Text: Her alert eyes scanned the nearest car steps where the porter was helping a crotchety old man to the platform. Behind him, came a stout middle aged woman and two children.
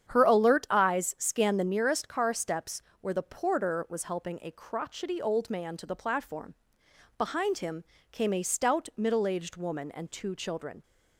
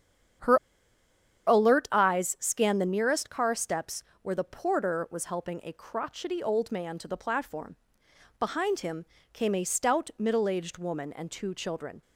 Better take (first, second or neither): first